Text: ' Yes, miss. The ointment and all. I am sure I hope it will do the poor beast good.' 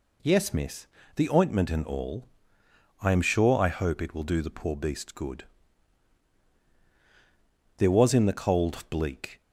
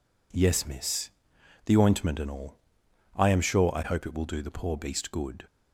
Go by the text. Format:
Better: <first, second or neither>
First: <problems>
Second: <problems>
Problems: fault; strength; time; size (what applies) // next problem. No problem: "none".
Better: second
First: goes on to say "There was in the cold bleak"; from 7.7 s on; 1.6 s long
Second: none